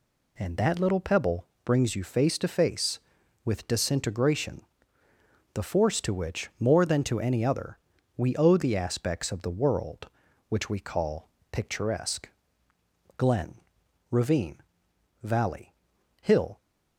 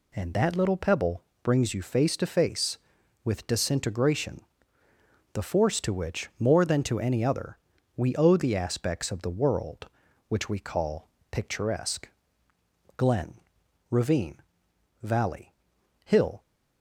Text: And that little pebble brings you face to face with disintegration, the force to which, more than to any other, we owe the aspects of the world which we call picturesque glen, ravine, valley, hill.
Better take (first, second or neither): neither